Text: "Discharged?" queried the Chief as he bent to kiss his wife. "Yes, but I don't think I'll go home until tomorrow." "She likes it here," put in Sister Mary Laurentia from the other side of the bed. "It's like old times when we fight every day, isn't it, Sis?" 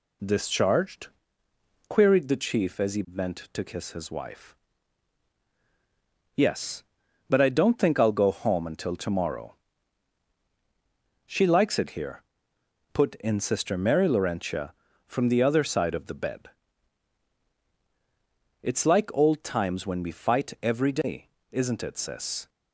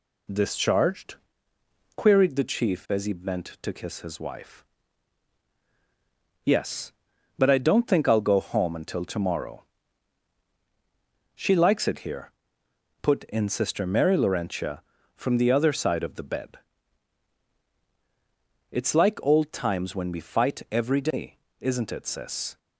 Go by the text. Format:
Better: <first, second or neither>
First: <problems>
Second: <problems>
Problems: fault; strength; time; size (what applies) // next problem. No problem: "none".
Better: neither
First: none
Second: none